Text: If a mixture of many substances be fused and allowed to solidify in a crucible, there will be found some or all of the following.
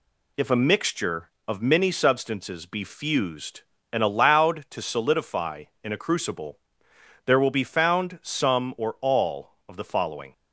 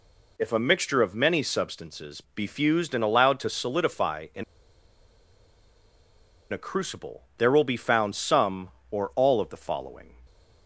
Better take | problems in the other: first | pauses between "in" and "a"; strong; at 4.4 s; 2.0 s long

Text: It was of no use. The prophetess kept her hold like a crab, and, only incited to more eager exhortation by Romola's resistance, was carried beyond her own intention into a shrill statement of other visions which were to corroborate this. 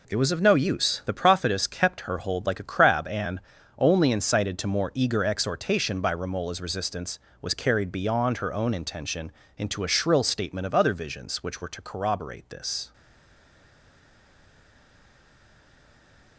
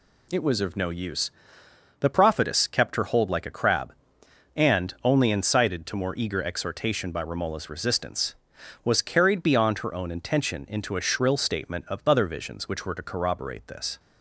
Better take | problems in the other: second | pauses between "intention" and "into"; slight; at 9.3 s; 0.26 s long // stays silent after the last word; strong; from 12.9 s on; 3.4 s long

